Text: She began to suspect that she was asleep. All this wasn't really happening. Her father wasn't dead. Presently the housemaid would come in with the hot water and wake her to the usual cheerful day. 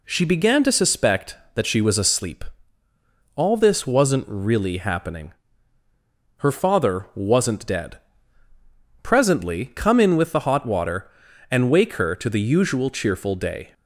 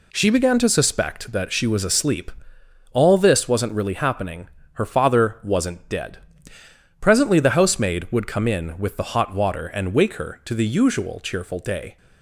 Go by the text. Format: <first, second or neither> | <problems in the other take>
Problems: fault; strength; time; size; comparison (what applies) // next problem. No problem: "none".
second | skips "the housemaid would"; at 9.7 s